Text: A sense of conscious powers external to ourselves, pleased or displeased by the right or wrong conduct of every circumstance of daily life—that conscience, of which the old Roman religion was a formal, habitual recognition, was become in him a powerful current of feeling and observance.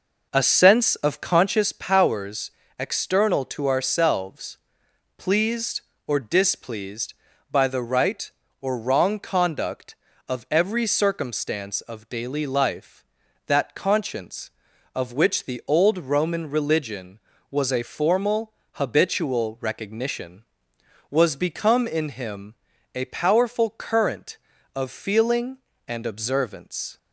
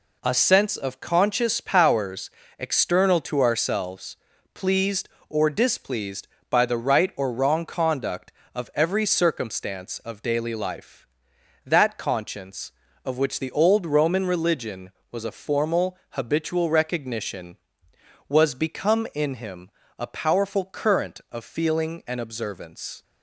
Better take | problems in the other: second | starts louder than the rest; noticeable; until 1.6 s; 5 dB // pauses between "powers" and "external"; slight; at 2.5 s; 0.28 s long; slight in the second // pauses between "him" and "a"; at 22.5 s; 0.40 s long; slight in the second

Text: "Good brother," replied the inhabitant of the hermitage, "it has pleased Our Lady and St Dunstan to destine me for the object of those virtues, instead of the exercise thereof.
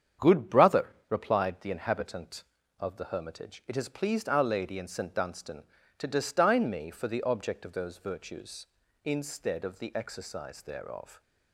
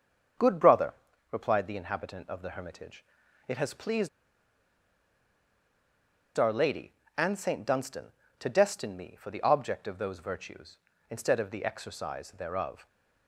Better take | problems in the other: first | starts louder than the rest; strong; until 1.7 s; 7 dB; strong in the first // pauses between "pleased" and "Our"; strong; at 4.0 s; 2.2 s long

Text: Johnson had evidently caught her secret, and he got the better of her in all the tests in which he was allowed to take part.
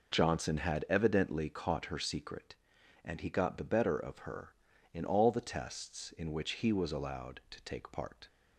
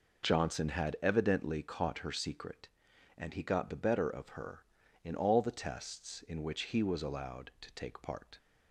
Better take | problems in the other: neither | none

